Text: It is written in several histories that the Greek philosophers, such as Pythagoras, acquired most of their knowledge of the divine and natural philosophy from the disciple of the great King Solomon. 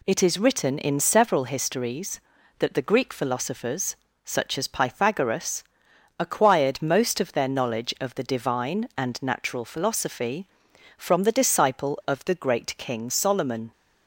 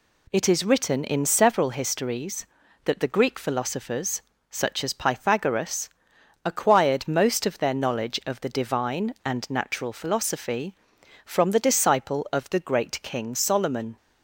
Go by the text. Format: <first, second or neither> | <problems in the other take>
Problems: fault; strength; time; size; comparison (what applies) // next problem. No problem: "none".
neither | none